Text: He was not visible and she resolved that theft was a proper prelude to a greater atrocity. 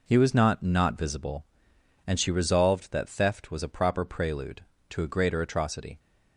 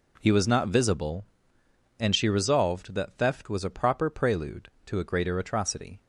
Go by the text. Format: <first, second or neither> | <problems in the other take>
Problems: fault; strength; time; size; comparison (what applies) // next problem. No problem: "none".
second | says "not" twice; at 0.6 s